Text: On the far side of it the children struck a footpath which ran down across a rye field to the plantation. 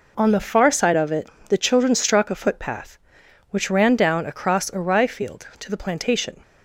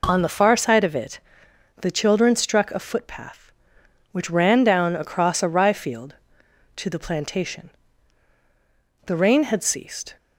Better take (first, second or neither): first